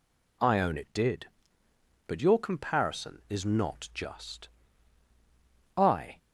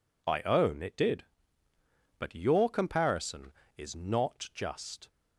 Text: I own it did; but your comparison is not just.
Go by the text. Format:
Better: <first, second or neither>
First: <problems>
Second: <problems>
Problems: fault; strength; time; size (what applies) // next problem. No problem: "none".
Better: second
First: goes on to say "I"; slight; from 5.7 s on; 0.38 s long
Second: none